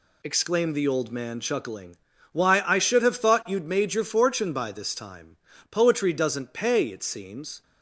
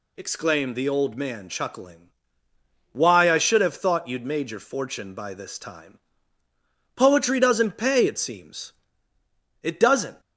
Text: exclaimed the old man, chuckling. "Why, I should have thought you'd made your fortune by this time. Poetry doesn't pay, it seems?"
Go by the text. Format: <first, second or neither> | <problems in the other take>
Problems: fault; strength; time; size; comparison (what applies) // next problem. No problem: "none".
first | goes on to say "It doesn't"; from 9.6 s on; 0.58 s long